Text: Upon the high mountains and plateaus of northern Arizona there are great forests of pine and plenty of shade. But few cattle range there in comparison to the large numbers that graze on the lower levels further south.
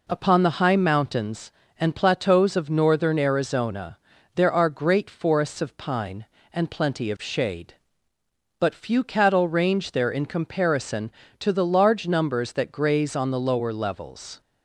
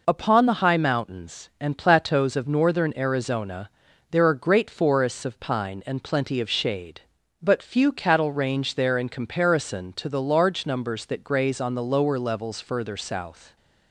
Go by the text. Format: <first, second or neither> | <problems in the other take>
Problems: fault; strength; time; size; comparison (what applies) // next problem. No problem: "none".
second | pauses between "Arizona" and "there"; at 3.9 s; 0.38 s long; also in the second // stops before "further south"; at 14.4 s